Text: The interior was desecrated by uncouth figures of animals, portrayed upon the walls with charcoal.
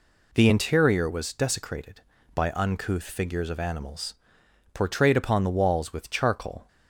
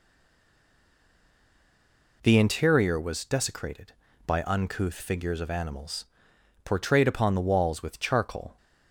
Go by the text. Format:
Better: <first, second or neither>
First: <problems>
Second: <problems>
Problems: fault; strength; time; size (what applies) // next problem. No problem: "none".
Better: first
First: none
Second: stays silent before the first word; until 2.2 s; 2.2 s long